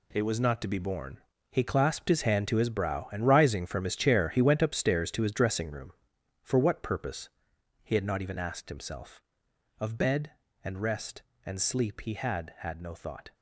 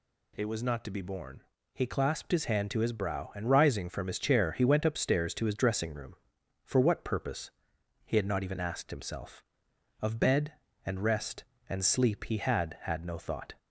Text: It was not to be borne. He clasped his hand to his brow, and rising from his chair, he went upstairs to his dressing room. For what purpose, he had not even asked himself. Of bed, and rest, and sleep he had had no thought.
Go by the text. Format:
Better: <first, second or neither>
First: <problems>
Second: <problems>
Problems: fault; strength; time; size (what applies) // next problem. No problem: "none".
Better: second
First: gets quieter; strong; throughout; 10.5 dB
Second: none